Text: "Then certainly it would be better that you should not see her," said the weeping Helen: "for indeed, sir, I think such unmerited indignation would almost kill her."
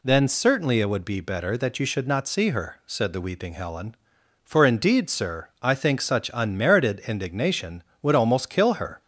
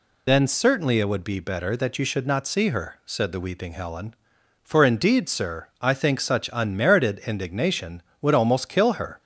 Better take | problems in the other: first | loses the start of "Then"; at 0.2 s; 55 ms

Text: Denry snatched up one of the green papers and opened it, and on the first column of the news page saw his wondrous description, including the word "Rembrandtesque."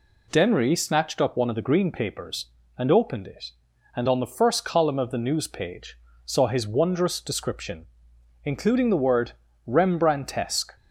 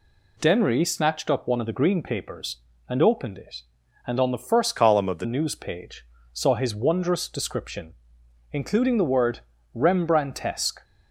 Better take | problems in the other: first | changes voice from "column" to "the"; from 4.7 to 5.2 s; 0.5 s long // pauses between "page" and "saw"; slight; at 6.0 s; 0.28 s long; slight in the first // pauses between "word" and "Rembrandtesque"; slight; at 9.3 s; 0.34 s long; slight in the first

